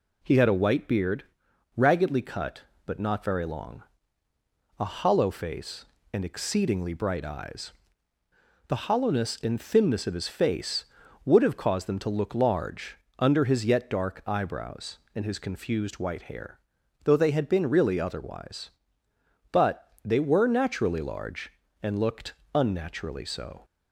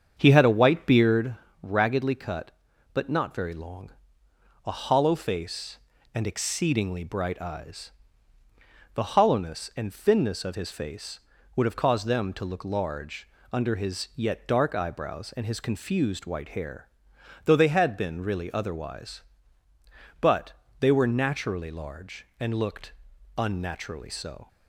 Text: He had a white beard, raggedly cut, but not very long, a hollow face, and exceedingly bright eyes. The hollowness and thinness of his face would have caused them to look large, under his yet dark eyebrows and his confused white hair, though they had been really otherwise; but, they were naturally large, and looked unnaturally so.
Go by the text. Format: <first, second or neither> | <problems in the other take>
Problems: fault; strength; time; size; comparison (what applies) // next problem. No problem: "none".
first | starts louder than the rest; strong; until 1.3 s; 7.5 dB // pauses between "looked" and "unnaturally"; noticeable; at 22.9 s; 0.46 s long; slight in the first